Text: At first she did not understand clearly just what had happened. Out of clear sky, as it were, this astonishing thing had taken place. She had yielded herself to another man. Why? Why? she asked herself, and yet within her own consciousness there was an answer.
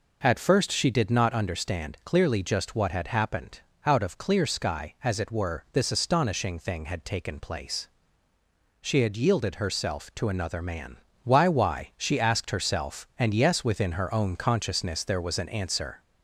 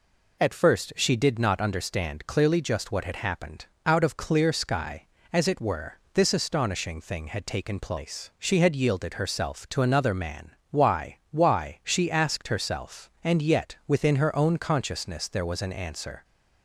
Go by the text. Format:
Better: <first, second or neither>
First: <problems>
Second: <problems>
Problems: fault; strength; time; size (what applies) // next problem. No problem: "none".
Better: second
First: says "yes" for "yet"; at 13.3 s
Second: none